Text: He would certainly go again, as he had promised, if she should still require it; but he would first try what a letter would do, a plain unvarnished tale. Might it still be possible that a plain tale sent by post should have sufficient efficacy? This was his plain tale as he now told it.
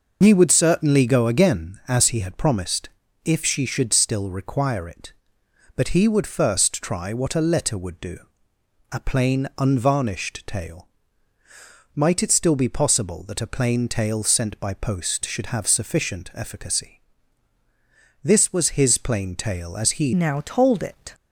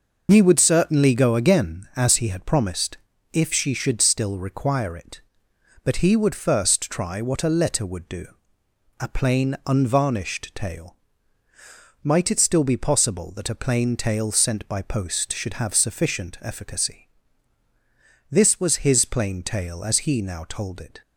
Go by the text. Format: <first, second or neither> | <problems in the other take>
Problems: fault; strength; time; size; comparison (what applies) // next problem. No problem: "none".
second | changes voice at "now"; from 20.1 s on; 1.0 s long